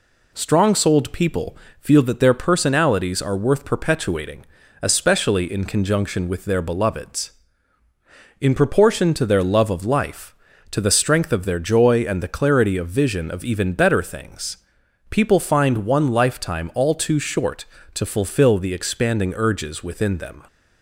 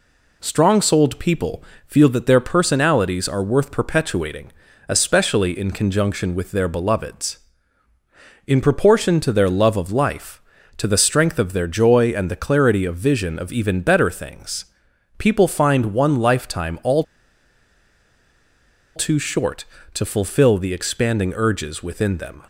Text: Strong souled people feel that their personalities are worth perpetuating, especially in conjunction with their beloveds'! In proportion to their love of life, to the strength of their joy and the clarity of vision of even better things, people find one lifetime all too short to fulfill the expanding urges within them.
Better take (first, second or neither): first